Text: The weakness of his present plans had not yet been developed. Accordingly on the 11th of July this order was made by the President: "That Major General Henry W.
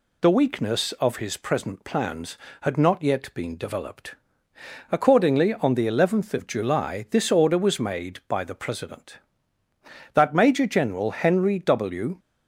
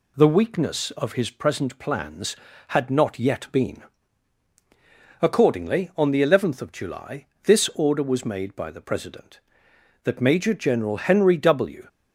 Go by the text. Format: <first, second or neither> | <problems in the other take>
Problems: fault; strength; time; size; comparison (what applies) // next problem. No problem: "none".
first | skips "developed"; at 4.5 s // pauses between "July" and "this"; slight; at 7.2 s; 0.18 s long